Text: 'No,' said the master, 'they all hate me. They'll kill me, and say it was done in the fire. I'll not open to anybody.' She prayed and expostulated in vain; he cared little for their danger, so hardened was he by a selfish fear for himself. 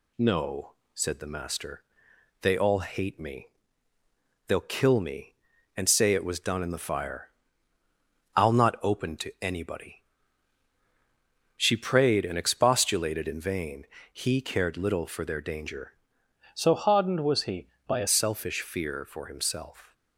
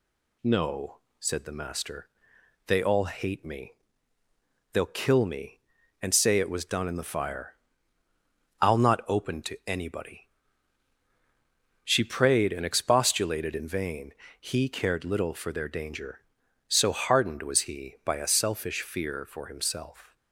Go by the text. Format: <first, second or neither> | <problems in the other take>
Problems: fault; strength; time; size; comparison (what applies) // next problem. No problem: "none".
second | changes voice from "so" to "a"; from 16.5 to 18.0 s; 1.5 s long